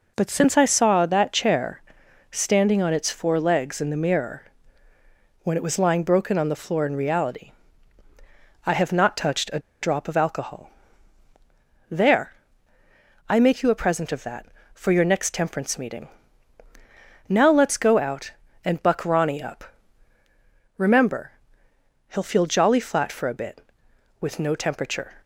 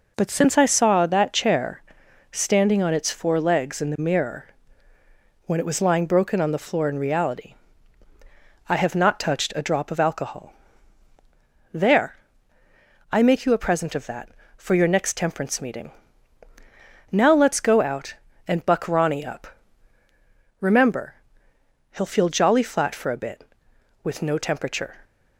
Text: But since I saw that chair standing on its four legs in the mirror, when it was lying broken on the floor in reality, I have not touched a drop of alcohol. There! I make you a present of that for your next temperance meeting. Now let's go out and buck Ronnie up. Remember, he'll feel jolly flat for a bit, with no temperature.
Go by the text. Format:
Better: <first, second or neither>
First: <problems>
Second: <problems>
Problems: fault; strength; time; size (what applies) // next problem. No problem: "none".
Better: second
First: pauses between "chair" and "standing"; noticeable; at 1.8 s; 0.50 s long // pauses between "a" and "drop"; slight; at 9.5 s; 0.22 s long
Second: pauses between "chair" and "standing"; noticeable; at 1.8 s; 0.50 s long